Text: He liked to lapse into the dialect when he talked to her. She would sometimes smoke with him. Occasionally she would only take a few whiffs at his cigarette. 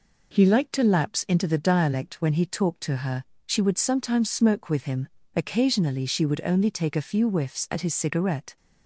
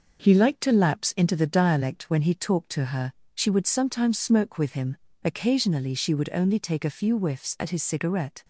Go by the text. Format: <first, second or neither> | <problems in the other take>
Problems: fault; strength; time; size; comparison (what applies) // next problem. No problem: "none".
first | gets quieter; throughout; 3.5 dB